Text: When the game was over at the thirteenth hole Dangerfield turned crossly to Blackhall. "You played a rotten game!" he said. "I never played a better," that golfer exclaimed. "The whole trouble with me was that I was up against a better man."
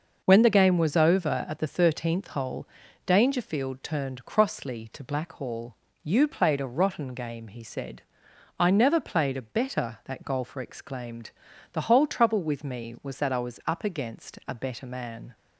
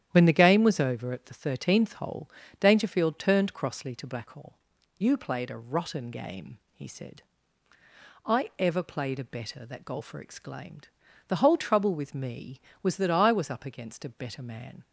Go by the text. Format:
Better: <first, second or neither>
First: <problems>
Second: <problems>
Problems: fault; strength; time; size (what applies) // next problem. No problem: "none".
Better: first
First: starts louder than the rest; noticeable; until 1.2 s; 6 dB // pauses between "hole" and "Dangerfield"; at 2.6 s; 0.38 s long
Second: starts louder than the rest; strong; until 1.1 s; 10.5 dB // pauses between "hole" and "Dangerfield"; slight; at 2.2 s; 0.30 s long // says "ever" for "never"; at 8.5 s